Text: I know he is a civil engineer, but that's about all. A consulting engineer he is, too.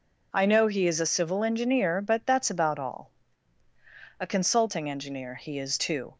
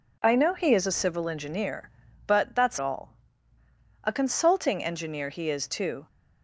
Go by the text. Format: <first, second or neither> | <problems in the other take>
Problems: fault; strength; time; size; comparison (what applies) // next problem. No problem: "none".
first | skips "about"; at 2.7 s